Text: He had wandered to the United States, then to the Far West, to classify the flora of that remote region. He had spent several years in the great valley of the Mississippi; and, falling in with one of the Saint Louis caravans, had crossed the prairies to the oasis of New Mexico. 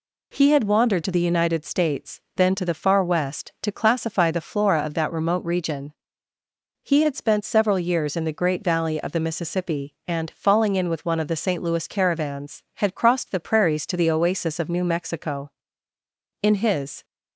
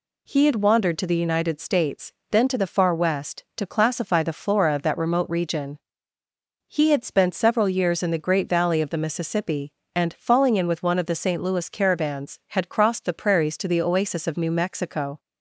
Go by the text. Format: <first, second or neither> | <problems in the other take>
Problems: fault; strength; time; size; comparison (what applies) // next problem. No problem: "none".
second | goes on to say "In his"; noticeable; from 16.4 s on; 0.62 s long